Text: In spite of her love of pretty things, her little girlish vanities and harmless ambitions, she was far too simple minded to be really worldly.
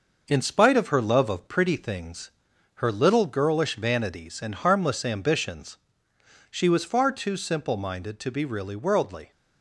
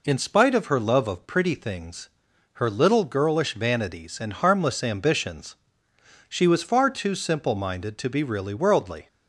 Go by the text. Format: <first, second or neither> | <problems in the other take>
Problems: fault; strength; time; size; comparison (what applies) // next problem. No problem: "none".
second | gets quieter; noticeable; throughout; 4.5 dB